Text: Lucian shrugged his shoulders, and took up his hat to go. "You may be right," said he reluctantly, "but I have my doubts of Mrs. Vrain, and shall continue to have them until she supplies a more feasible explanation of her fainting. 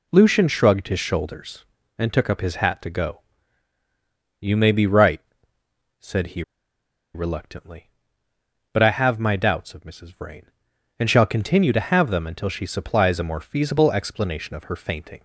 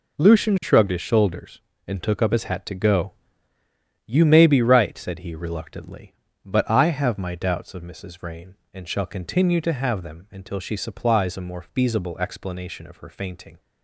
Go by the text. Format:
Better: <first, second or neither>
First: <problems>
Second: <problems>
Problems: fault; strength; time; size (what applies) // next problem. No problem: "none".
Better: second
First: pauses between "he" and "reluctantly"; noticeable; at 6.4 s; 0.72 s long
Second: none